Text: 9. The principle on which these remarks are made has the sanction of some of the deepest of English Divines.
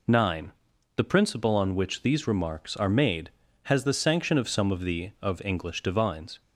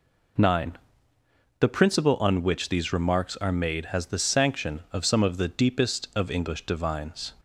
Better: second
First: skips "deepest"; at 5.1 s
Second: none

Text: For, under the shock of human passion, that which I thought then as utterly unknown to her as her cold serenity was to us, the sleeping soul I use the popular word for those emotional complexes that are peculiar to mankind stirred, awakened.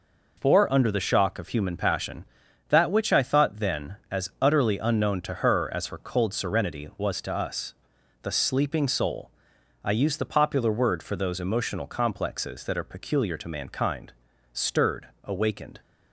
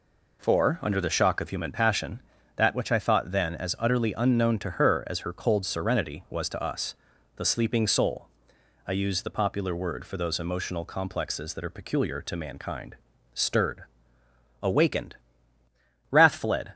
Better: first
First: pauses between "soul" and "I"; noticeable; at 9.3 s; 0.54 s long // pauses between "mankind" and "stirred"; at 14.1 s; 0.40 s long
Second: pauses between "soul" and "I"; noticeable; at 8.2 s; 0.60 s long // pauses between "mankind" and "stirred"; slight; at 12.9 s; 0.36 s long // goes on to say "Wrath fled"; noticeable; from 16.1 s on; 0.62 s long

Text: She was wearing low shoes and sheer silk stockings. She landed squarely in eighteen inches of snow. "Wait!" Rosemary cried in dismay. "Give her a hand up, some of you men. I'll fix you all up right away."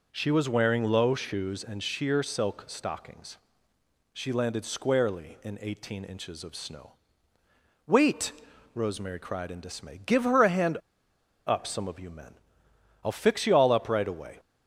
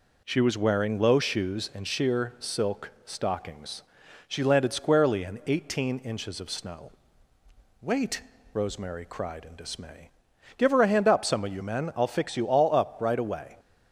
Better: second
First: pauses between "hand" and "up"; noticeable; at 10.7 s; 0.69 s long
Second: none

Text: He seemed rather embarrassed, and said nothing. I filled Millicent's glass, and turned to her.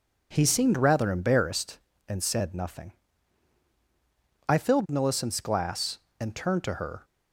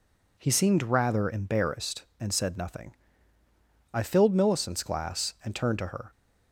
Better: neither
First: none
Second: none

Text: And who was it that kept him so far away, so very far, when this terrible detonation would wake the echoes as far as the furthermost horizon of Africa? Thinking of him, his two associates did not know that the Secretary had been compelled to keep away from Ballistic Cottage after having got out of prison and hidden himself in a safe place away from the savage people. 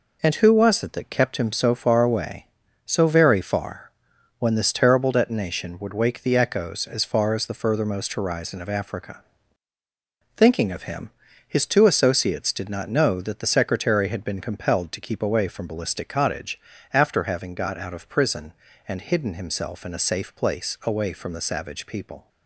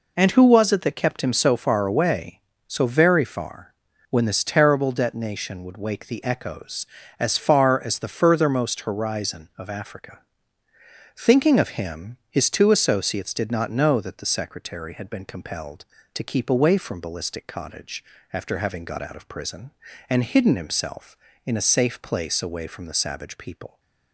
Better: neither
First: pauses between "Cottage" and "after"; slight; at 16.5 s; 0.34 s long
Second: pauses between "Cottage" and "after"; slight; at 18.0 s; 0.30 s long

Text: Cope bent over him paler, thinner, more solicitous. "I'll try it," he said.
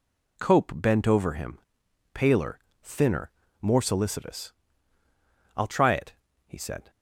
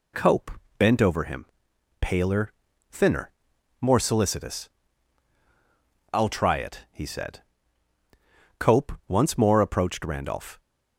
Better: first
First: pauses between "him" and "paler"; noticeable; at 1.5 s; 0.54 s long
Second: pauses between "Cope" and "bent"; slight; at 0.5 s; 0.26 s long // pauses between "him" and "paler"; noticeable; at 1.4 s; 0.56 s long // goes on to say "Cope once more approached Randolph"; strong; from 8.6 s on; 2.0 s long

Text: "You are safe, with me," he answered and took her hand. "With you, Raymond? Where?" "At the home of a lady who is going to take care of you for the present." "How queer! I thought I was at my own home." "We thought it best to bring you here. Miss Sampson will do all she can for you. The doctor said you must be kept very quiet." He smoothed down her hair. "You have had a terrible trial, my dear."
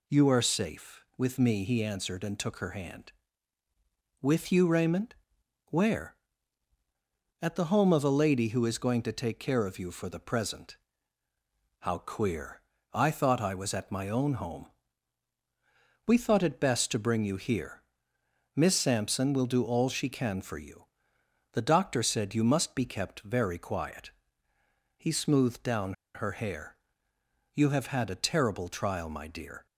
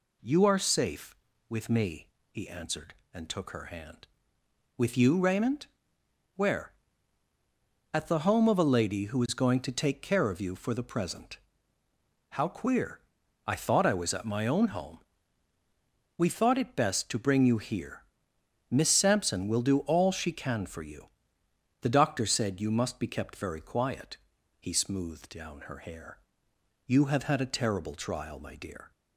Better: second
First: pauses between "down" and "her"; slight; at 25.9 s; 0.20 s long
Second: none

